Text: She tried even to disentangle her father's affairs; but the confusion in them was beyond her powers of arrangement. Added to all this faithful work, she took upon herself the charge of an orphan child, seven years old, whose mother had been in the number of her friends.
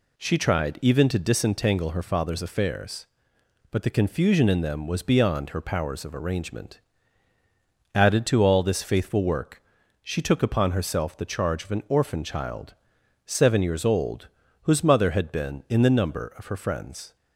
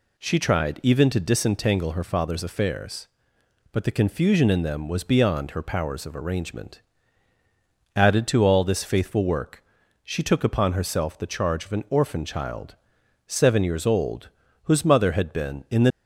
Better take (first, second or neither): first